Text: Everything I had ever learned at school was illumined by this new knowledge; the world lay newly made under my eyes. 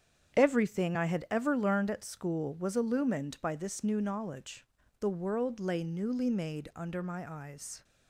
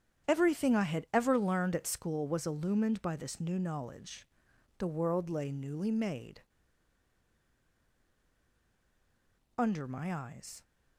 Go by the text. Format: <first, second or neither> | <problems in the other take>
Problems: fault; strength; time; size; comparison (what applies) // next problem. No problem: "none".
first | starts louder than the rest; strong; until 1.3 s; 8.5 dB; strong in the first // pauses between "made" and "under"; strong; at 6.3 s; 3.1 s long